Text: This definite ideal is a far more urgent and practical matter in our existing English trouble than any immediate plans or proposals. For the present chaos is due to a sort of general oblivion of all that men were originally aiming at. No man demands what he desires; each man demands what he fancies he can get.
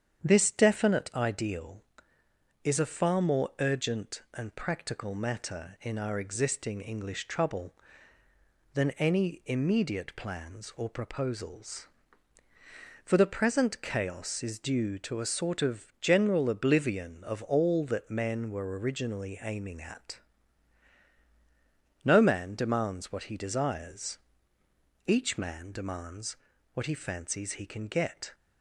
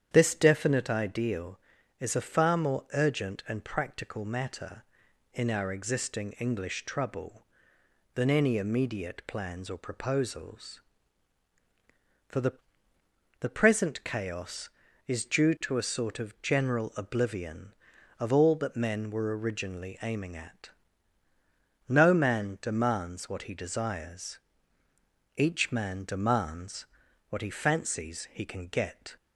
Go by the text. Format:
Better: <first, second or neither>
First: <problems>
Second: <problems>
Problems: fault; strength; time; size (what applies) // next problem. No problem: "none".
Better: first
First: starts louder than the rest; strong; until 1.3 s; 8.5 dB // pauses between "demands" and "what"; at 26.3 s; 0.38 s long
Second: starts louder than the rest; strong; until 1.1 s; 9 dB // says "the" twice; at 13.4 s // pauses between "demands" and "what"; at 26.8 s; 0.42 s long